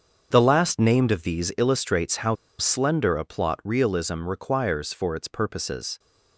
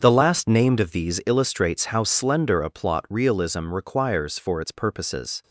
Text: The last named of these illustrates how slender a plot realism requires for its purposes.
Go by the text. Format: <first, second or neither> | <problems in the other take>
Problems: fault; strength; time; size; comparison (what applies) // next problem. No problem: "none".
second | starts louder than the rest; until 1.3 s; 7 dB; also in the second // pauses between "how" and "slender"; slight; at 2.3 s; 0.23 s long